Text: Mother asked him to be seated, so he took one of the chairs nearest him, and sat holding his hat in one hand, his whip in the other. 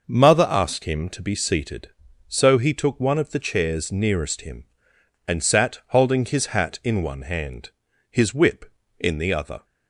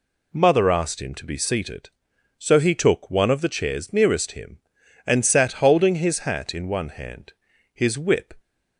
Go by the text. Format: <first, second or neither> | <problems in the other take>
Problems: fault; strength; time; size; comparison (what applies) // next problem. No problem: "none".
first | stops before "in the other"; at 8.3 s